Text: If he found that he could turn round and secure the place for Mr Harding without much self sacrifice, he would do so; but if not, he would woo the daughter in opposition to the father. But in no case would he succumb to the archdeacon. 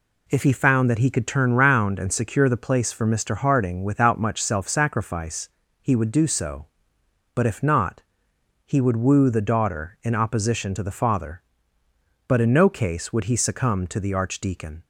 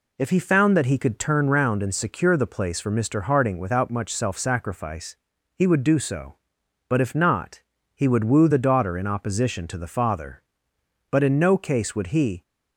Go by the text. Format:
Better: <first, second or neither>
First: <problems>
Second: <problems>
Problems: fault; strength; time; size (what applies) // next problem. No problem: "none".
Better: first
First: none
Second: stops before "succumb to the archdeacon"; at 12.4 s